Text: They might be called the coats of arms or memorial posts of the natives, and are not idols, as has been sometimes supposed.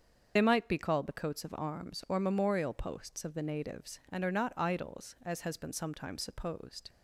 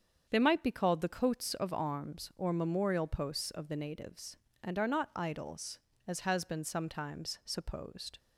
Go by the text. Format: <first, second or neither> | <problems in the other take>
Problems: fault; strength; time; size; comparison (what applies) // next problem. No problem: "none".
second | loses the start of "They"; at 0.3 s; 45 ms // starts louder than the rest; until 1.3 s; 7 dB; strong in the second